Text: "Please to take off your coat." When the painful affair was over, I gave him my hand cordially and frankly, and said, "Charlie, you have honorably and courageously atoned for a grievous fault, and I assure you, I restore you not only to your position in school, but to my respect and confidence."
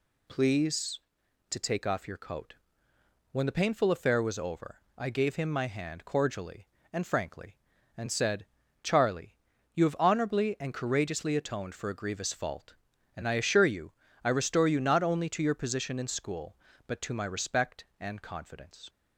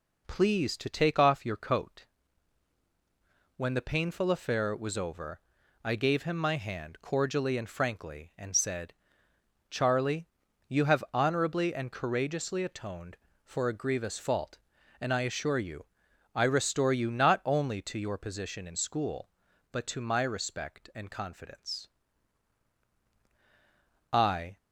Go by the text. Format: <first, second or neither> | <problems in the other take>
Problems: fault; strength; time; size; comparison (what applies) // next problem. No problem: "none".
first | goes on to say "I"; slight; from 24.1 s on; 0.46 s long